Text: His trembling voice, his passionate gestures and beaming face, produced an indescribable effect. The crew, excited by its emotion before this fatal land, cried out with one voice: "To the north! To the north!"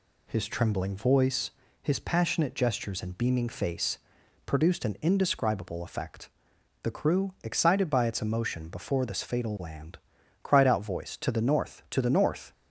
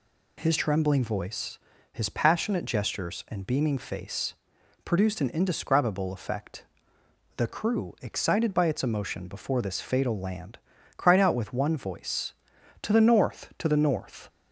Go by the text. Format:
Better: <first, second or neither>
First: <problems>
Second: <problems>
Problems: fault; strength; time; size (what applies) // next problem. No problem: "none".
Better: second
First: skips "with one"; at 10.8 s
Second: none